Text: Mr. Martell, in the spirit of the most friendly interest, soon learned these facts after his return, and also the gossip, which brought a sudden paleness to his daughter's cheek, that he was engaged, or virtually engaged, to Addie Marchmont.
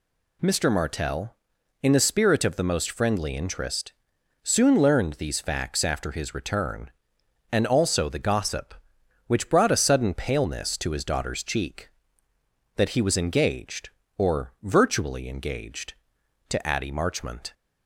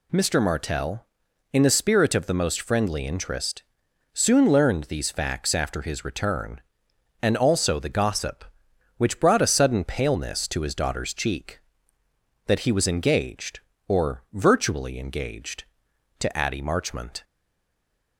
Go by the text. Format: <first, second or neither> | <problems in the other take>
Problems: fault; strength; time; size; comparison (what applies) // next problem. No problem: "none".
first | stays silent after the last word; slight; from 17.2 s on; 0.9 s long